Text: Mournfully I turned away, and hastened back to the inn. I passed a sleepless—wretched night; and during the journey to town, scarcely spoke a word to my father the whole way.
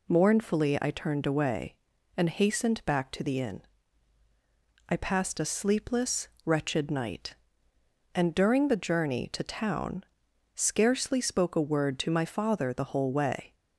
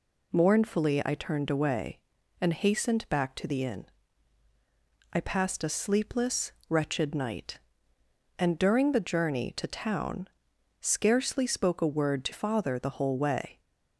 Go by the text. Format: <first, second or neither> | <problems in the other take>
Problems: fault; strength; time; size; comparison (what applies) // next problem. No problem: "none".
first | skips "my"; at 12.3 s